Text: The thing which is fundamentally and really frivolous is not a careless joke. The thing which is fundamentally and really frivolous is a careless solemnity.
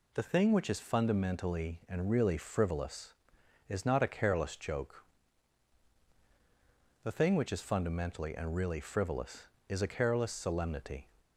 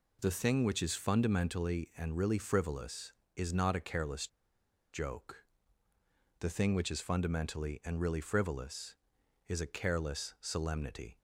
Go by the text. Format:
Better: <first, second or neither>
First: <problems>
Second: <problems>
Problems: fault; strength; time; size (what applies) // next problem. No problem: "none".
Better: first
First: none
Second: pauses between "careless" and "joke"; noticeable; at 4.2 s; 0.65 s long